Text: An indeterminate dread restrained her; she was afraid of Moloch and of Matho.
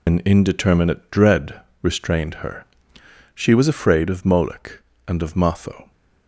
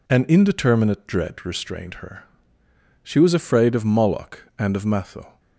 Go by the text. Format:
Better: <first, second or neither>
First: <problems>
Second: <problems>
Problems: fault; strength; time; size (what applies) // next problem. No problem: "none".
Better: second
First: loses the start of "An"; at 0.0 s; 70 ms // pauses between "dread" and "restrained"; slight; at 1.6 s; 0.22 s long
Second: none